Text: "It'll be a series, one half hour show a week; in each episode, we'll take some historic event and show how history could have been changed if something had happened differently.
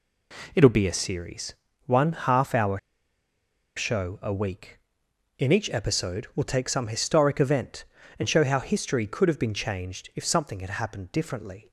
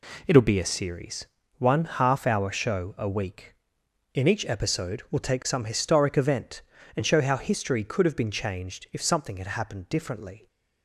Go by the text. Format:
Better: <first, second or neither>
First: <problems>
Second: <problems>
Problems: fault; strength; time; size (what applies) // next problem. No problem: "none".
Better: second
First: pauses between "hour" and "show"; noticeable; at 2.7 s; 0.96 s long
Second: none